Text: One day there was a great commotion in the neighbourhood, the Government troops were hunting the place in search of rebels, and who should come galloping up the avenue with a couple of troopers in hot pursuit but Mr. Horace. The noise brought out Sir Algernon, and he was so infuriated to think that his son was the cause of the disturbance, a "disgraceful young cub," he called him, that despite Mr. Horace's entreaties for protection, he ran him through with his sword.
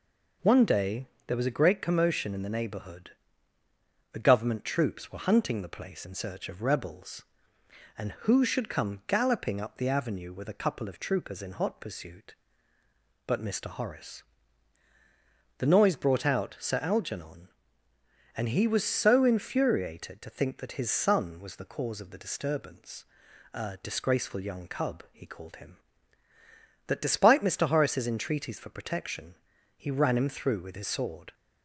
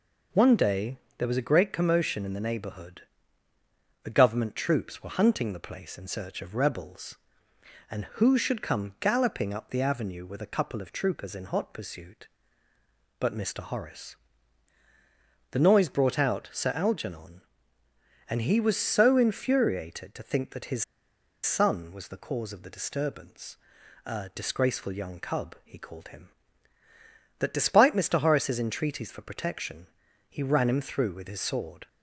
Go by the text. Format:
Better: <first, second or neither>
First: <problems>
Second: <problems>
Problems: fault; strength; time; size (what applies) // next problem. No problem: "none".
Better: first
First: pauses between "day" and "there"; slight; at 1.0 s; 0.20 s long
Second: pauses between "day" and "there"; slight; at 0.9 s; 0.20 s long // pauses between "his" and "son"; noticeable; at 20.8 s; 0.59 s long